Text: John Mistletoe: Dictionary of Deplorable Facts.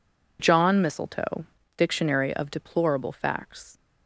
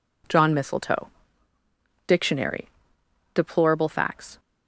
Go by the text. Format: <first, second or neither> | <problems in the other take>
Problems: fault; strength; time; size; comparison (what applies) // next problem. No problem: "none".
first | skips "of"; at 3.0 s